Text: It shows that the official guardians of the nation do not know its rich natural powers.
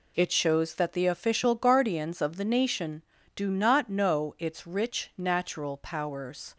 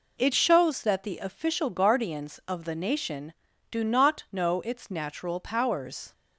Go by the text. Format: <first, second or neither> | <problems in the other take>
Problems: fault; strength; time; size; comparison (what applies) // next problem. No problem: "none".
first | skips "rich"; at 4.8 s